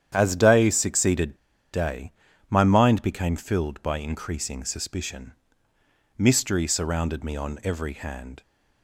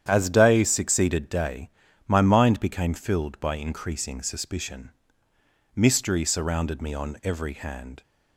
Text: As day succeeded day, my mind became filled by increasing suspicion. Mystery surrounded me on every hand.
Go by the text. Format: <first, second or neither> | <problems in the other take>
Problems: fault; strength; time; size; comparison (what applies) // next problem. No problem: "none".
second | starts louder than the rest; strong; until 1.1 s; 9.5 dB; strong in the second // pauses between "succeeded" and "day"; at 1.3 s; 0.37 s long